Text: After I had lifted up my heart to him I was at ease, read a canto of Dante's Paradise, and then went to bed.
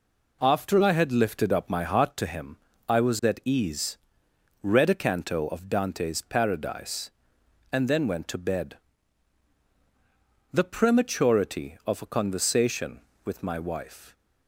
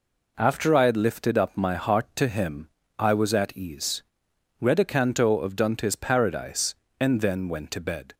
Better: second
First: pauses between "him" and "I"; slight; at 2.5 s; 0.28 s long // goes on to say "The prematurity of a conversation with my wife"; strong; from 10.5 s on; 3.6 s long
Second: pauses between "him" and "I"; slight; at 2.6 s; 0.32 s long

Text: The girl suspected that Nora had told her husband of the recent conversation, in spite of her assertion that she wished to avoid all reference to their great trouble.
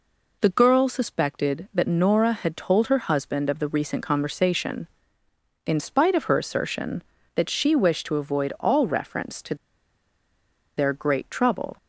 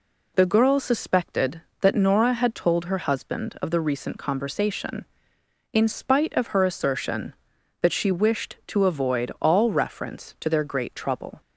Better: second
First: pauses between "to" and "their"; at 9.5 s; 1.2 s long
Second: none

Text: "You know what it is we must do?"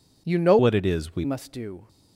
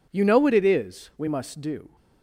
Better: second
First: changes voice from "what" to "we"; from 0.5 to 1.2 s; 0.7 s long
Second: none

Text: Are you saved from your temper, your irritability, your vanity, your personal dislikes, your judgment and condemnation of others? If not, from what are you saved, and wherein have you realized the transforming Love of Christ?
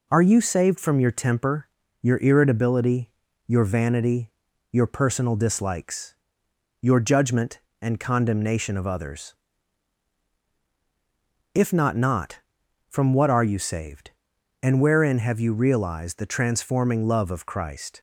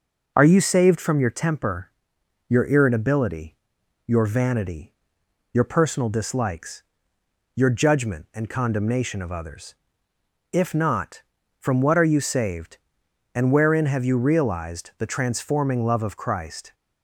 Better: second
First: says "not" twice; at 11.9 s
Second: none

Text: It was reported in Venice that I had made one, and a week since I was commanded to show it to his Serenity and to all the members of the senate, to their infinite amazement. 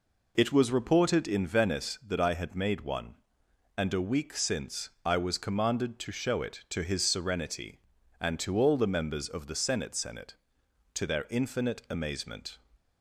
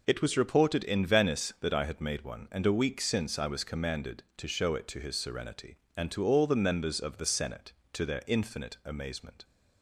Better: second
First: says "senate" twice; at 9.9 s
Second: none

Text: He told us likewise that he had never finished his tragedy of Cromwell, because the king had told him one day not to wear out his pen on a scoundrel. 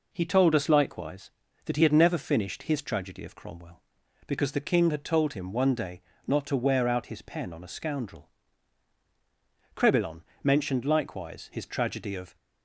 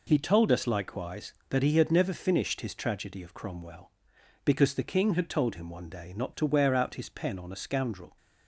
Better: second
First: pauses between "day" and "not"; slight; at 6.0 s; 0.26 s long // goes on to say "Crebillon mentioned likewise his tragedy of"; strong; from 9.7 s on; 2.6 s long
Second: none

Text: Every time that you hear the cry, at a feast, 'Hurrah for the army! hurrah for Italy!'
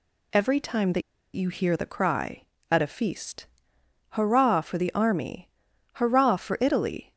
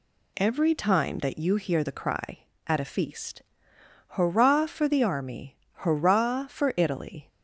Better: second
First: pauses between "that" and "you"; slight; at 1.0 s; 0.33 s long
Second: none

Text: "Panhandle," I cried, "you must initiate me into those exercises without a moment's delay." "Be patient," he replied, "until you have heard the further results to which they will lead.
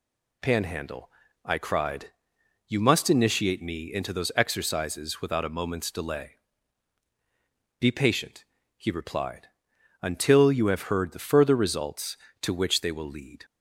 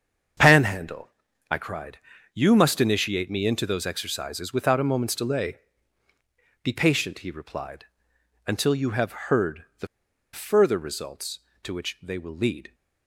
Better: first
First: none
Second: starts louder than the rest; strong; until 1.7 s; 7.5 dB // pauses between "heard" and "the"; slight; at 9.6 s; 0.16 s long // pauses between "the" and "further"; noticeable; at 9.8 s; 0.47 s long

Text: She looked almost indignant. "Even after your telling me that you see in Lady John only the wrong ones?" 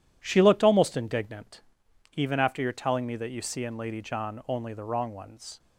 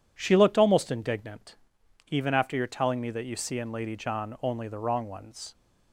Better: second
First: gets quieter; strong; throughout; 7.5 dB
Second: none

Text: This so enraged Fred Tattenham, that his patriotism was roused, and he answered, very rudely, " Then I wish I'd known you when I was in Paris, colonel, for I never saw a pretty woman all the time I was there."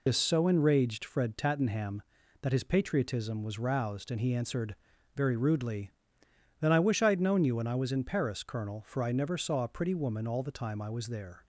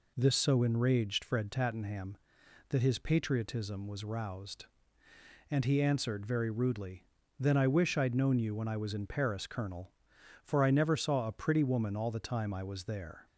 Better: second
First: loses the start of "This"; at 0.0 s; 65 ms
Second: none

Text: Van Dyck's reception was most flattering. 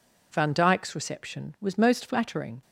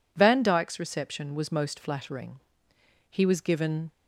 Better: first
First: none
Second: goes on to say "He was given"; noticeable; from 3.1 s on; 0.82 s long

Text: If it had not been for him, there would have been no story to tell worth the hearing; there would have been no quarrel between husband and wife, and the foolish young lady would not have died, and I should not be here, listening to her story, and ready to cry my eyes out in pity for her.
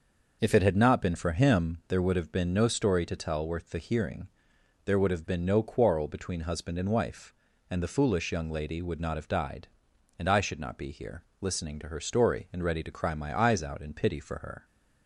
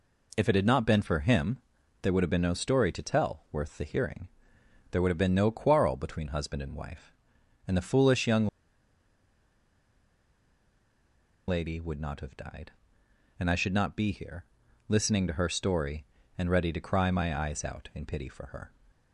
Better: first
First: none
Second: pauses between "young" and "lady"; strong; at 8.4 s; 3.0 s long

